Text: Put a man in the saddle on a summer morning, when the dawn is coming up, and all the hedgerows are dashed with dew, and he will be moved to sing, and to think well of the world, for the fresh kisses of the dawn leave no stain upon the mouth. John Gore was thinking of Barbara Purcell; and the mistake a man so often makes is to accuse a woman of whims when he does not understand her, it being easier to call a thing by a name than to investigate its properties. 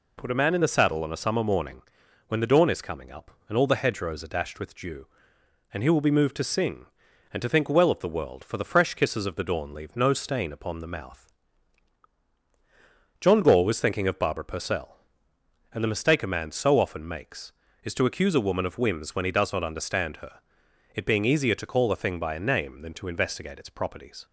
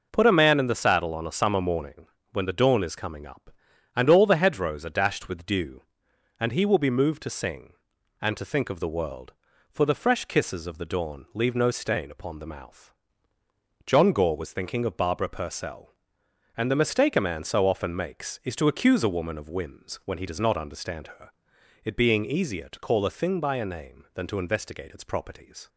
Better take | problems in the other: first | skips "well"; at 8.6 s

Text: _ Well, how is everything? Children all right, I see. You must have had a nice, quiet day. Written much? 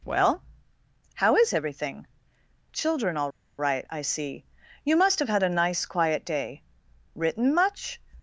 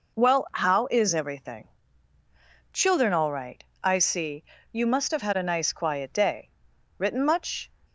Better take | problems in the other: second | pauses between "all" and "right"; slight; at 3.3 s; 0.28 s long

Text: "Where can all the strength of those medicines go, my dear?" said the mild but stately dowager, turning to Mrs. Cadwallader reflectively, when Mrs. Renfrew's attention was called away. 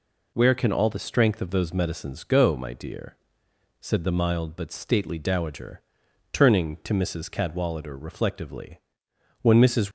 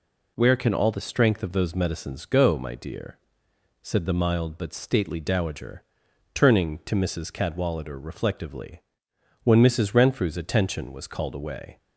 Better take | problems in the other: second | stops before "Renfrew's attention was called away"; at 9.8 s

